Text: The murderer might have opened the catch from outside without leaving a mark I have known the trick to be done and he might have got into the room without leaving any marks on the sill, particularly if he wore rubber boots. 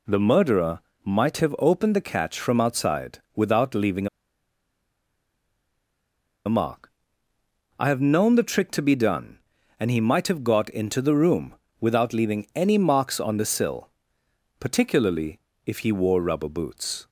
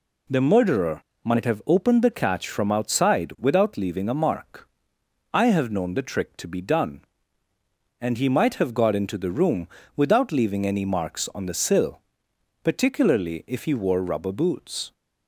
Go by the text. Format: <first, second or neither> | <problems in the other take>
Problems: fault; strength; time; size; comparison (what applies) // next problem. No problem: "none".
second | pauses between "murderer" and "might"; slight; at 0.7 s; 0.26 s long; slight in the second // pauses between "outside" and "without"; slight; at 3.1 s; 0.16 s long // pauses between "leaving" and "a"; strong; at 4.0 s; 2.3 s long // pauses between "mark" and "I"; noticeable; at 6.9 s; 0.88 s long; noticeable in the second // pauses between "room" and "without"; slight; at 11.5 s; 0.26 s long; slight in the second // pauses between "particularly" and "if"; slight; at 15.3 s; 0.28 s long